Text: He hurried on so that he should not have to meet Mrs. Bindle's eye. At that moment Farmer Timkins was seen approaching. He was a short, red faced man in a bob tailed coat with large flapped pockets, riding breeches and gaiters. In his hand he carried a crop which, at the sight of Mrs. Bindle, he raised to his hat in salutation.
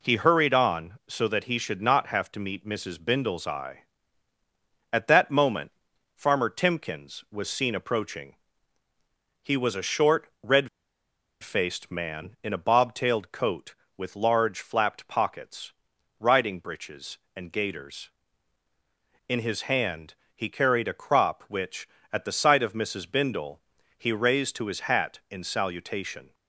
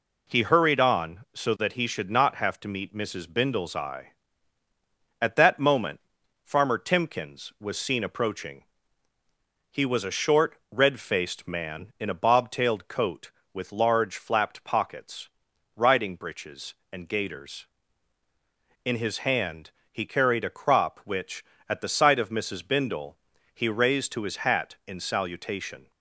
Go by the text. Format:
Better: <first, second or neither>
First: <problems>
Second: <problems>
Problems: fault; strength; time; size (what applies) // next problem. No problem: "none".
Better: second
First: pauses between "moment" and "Farmer"; noticeable; at 5.6 s; 0.46 s long // pauses between "red" and "faced"; noticeable; at 10.6 s; 0.75 s long // pauses between "hand" and "he"; slight; at 20.1 s; 0.20 s long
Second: pauses between "moment" and "Farmer"; noticeable; at 5.9 s; 0.46 s long // pauses between "hand" and "he"; slight; at 19.7 s; 0.20 s long